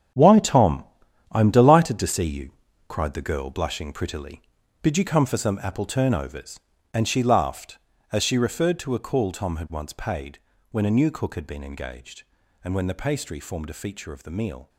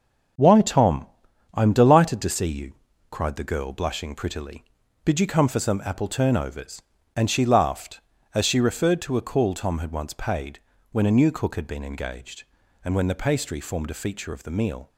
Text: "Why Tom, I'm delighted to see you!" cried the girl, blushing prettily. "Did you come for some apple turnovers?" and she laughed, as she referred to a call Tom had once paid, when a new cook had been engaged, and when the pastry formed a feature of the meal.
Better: second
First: gets quieter; strong; throughout; 11.5 dB // starts louder than the rest; strong; until 1.6 s; 8.5 dB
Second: starts louder than the rest; until 1.8 s; 6.5 dB

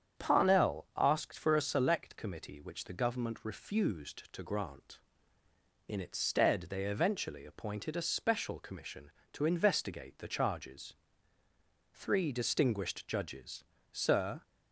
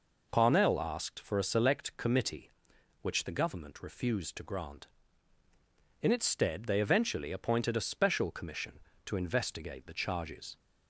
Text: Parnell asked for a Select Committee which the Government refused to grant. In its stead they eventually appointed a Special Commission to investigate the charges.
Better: second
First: starts louder than the rest; strong; until 1.2 s; 8 dB // goes on to say "Three distinguished Judges Sir"; strong; from 11.9 s on; 2.5 s long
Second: none

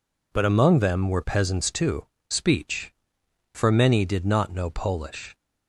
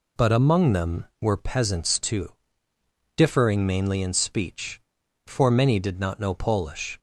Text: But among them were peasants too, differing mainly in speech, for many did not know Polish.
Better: second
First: skips "differing mainly in"; at 2.1 s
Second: none

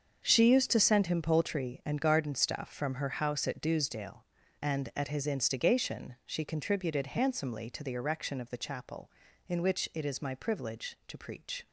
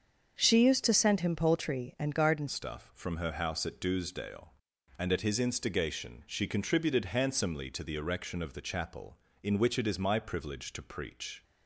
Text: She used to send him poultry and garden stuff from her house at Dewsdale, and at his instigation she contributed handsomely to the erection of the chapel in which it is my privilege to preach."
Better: first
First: starts louder than the rest; until 1.2 s; 6.5 dB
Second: starts louder than the rest; until 1.4 s; 7 dB // changes voice at "stuff"; from 2.4 s on; 9.0 s long

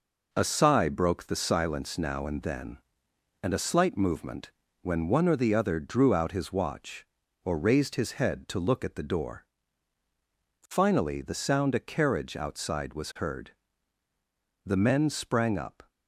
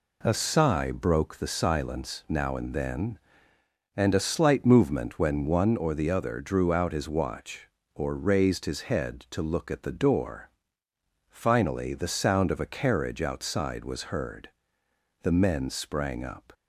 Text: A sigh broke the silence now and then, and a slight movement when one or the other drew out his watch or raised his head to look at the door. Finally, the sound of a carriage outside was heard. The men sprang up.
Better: second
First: pauses between "movement" and "when"; slight; at 4.5 s; 0.30 s long // skips "of"; at 11.7 s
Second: none

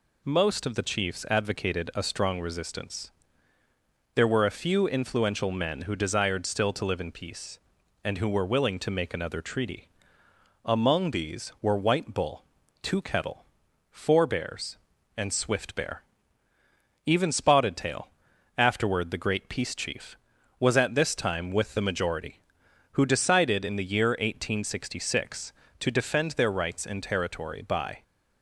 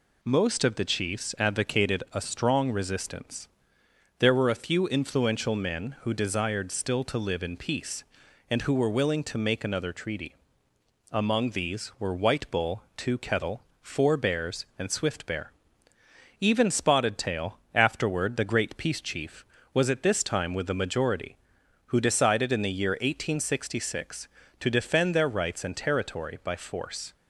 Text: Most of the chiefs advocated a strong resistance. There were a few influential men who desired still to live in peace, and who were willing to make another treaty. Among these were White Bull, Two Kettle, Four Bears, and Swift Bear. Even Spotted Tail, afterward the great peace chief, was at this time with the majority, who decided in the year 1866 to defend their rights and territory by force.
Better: second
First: stops before "force"; at 28.0 s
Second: none

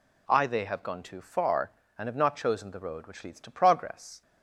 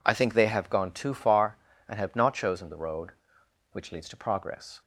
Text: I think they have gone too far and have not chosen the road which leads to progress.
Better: second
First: skips "think"; at 0.4 s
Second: none

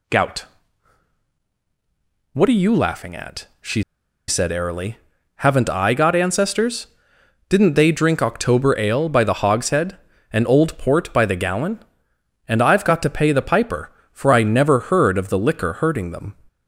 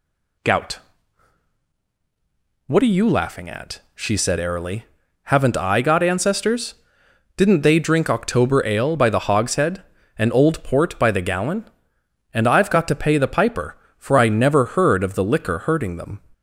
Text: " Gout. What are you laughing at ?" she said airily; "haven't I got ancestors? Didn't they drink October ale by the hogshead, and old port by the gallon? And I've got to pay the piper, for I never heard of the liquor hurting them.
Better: second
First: pauses between "she" and "said"; at 3.8 s; 0.45 s long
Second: none

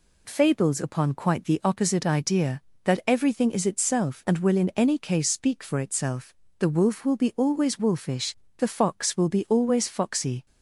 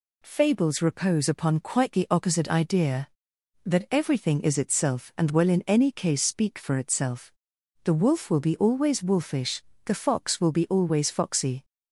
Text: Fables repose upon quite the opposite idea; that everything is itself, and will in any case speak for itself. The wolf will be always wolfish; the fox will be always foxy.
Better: second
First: skips "repose"; at 0.7 s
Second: none

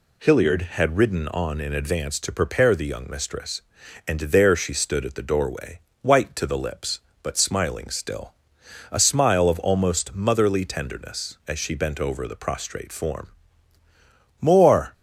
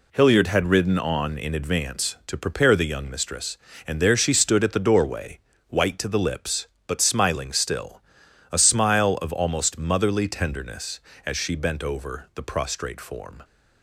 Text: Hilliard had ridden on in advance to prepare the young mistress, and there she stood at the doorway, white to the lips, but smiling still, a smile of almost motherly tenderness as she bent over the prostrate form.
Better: second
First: goes on to say "More"; from 14.4 s on; 0.52 s long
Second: none

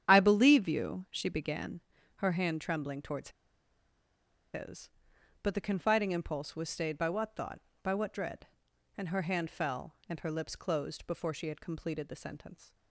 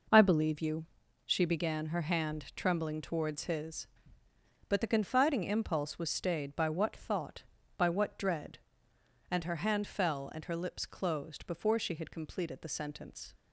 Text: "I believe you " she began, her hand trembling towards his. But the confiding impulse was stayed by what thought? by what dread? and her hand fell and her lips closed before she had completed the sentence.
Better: second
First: starts louder than the rest; strong; until 1.1 s; 9.5 dB // pauses between "towards" and "his"; strong; at 3.2 s; 1.2 s long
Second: none

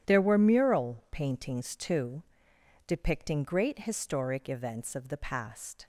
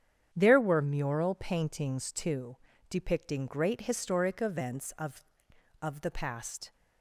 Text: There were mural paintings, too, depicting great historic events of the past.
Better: first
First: starts louder than the rest; strong; until 1.1 s; 10 dB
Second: starts louder than the rest; strong; until 1.3 s; 9 dB // says "of" twice; at 5.8 s

